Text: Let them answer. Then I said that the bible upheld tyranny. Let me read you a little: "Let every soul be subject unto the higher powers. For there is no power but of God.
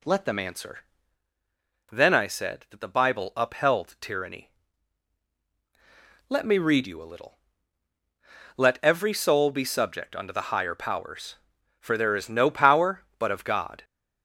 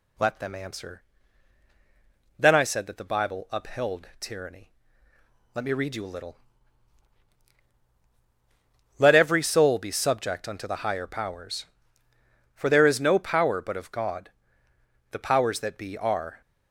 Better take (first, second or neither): first